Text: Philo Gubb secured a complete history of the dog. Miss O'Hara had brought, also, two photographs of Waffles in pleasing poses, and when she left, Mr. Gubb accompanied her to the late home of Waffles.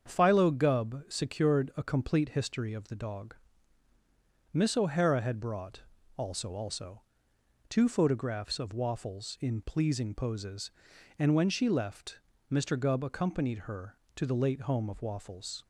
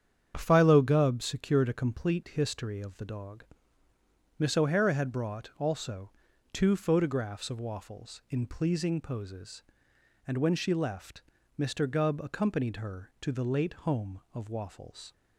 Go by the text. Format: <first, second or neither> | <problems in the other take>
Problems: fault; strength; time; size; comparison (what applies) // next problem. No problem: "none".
second | starts louder than the rest; strong; until 1.1 s; 7 dB; strong in the second // says "also" twice; at 6.5 s